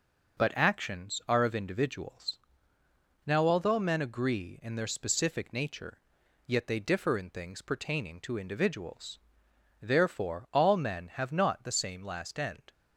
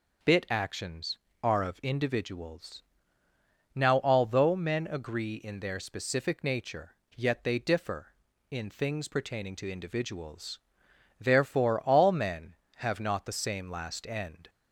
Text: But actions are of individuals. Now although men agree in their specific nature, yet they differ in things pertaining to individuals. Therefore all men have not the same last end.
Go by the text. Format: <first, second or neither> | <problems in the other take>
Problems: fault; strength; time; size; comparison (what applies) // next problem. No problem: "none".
first | starts louder than the rest; until 1.5 s; 6 dB; also in the first // says "Bit" for "But"; at 0.2 s